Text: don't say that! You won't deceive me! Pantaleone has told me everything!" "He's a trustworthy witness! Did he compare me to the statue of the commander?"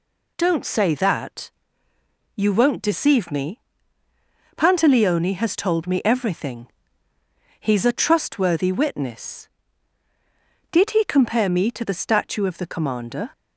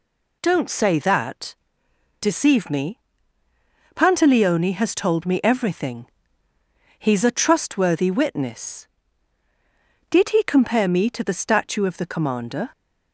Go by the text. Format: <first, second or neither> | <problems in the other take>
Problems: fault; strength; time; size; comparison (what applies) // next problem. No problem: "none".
first | skips "You won't"; at 1.8 s